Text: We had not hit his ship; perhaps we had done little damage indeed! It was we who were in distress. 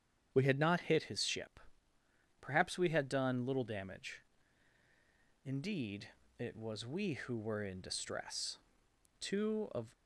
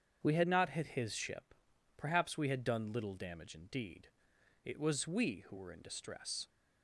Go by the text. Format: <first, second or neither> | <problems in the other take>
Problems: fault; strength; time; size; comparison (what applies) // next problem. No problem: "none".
second | starts louder than the rest; strong; until 1.3 s; 8.5 dB; strong in the second // pauses between "damage" and "indeed"; at 4.2 s; 1.2 s long // goes on to say "Two of"; noticeable; from 9.1 s on; 0.66 s long